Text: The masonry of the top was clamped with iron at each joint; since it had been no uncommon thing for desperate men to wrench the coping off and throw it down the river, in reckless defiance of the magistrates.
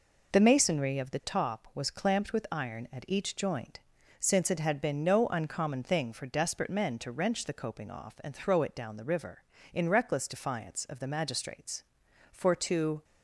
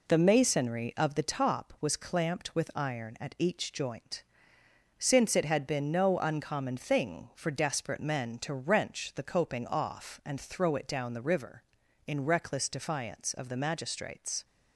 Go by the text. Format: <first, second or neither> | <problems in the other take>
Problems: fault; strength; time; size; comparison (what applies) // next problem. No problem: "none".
second | goes on to say "For to"; noticeable; from 12.3 s on; 0.72 s long